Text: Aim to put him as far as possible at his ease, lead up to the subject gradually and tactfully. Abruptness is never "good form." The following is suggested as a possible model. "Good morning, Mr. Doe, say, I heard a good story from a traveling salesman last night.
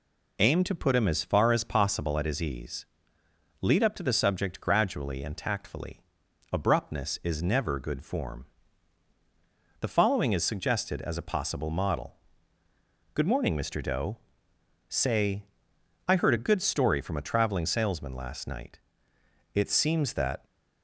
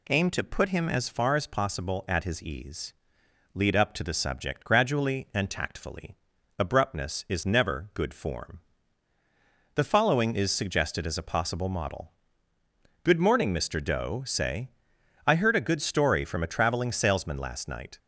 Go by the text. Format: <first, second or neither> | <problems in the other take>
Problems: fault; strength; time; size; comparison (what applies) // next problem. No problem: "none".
second | goes on to say "It seems that"; noticeable; from 19.5 s on; 0.90 s long